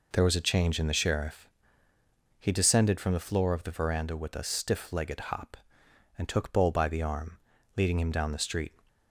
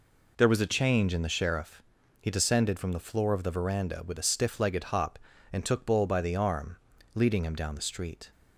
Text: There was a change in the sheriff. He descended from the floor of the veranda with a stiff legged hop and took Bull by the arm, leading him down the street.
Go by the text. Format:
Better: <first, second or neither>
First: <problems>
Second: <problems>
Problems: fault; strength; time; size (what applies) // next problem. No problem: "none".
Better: neither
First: none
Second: none